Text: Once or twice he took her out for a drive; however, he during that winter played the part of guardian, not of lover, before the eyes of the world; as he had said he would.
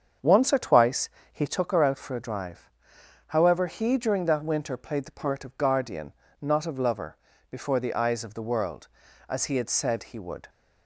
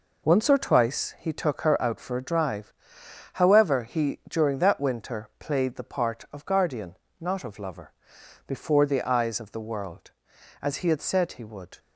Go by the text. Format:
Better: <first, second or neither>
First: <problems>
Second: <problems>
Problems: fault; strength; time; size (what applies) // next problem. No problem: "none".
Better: second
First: starts louder than the rest; strong; until 1.6 s; 7 dB // pauses between "twice" and "he"; slight; at 1.0 s; 0.24 s long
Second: none